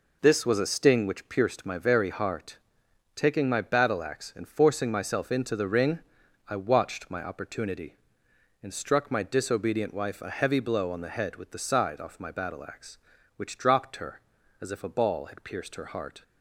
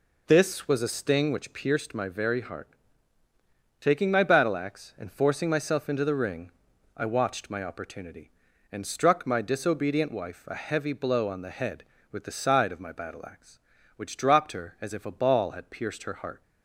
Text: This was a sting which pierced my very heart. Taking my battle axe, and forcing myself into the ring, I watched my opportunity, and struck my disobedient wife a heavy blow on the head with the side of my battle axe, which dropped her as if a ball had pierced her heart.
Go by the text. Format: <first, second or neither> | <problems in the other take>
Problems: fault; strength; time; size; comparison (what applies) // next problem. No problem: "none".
second | says "off" for "of"; at 12.0 s